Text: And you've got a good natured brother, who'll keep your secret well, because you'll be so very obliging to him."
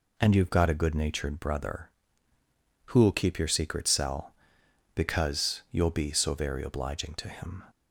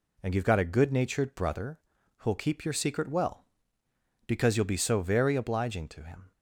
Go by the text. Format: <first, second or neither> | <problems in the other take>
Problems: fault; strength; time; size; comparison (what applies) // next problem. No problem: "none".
second | says "cell" for "well"; at 3.8 s